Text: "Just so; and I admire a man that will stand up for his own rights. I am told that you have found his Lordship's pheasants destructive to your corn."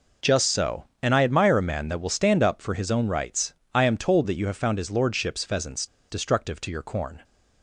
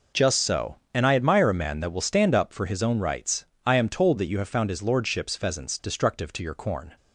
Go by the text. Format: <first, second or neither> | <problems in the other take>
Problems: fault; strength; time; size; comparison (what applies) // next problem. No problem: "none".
second | pauses between "pheasants" and "destructive"; slight; at 5.8 s; 0.24 s long